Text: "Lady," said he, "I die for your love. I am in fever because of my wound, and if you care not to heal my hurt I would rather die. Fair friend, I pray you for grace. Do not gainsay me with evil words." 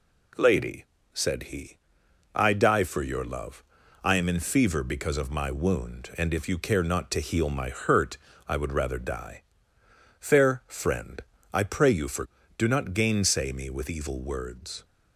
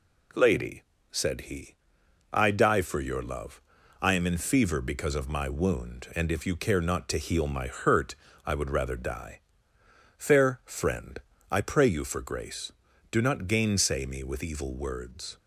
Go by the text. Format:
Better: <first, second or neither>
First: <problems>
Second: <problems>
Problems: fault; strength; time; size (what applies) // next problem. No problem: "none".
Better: second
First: pauses between "hurt" and "I"; slight; at 8.1 s; 0.30 s long // skips "grace"; at 12.4 s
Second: pauses between "hurt" and "I"; slight; at 8.1 s; 0.30 s long